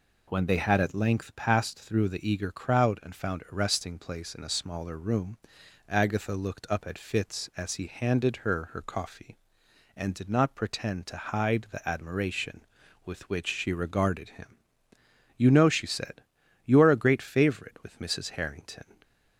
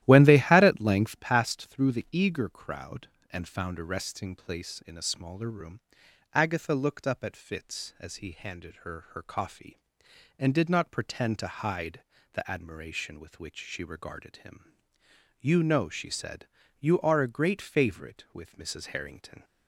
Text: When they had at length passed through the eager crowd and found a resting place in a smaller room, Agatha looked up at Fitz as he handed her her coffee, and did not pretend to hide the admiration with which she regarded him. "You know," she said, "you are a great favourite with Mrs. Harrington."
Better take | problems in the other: first | starts louder than the rest; strong; until 1.3 s; 13.5 dB // pauses between "hide" and "the"; slight; at 12.0 s; 0.30 s long

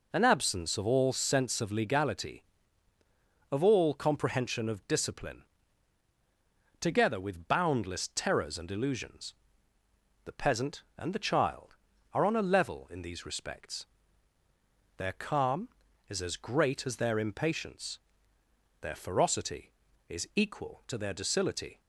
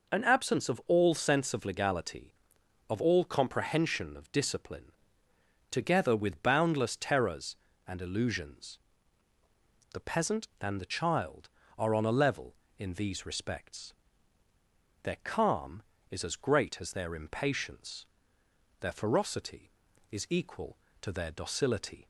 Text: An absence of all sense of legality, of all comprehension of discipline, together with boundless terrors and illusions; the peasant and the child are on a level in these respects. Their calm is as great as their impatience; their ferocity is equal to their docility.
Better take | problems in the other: neither | none

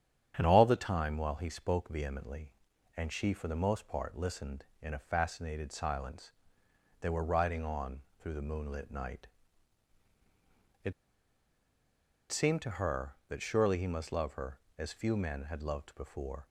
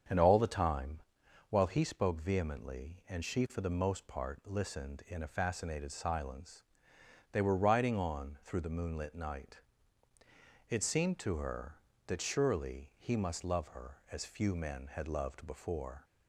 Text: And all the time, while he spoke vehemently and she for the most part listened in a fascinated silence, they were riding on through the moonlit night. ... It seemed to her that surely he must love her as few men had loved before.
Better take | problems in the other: second | starts louder than the rest; strong; until 1.3 s; 9 dB; strong in the second // pauses between "on" and "through"; slight; at 7.9 s; 0.22 s long // pauses between "It" and "seemed"; strong; at 10.9 s; 1.3 s long

